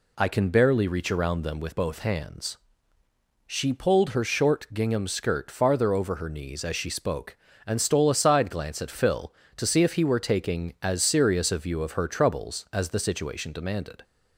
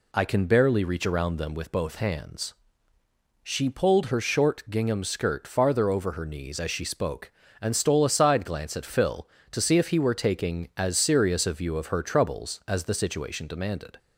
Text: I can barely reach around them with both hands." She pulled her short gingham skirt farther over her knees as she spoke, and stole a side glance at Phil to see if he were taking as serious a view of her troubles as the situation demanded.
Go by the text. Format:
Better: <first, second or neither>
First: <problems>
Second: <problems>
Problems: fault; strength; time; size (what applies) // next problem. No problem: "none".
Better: neither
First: none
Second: none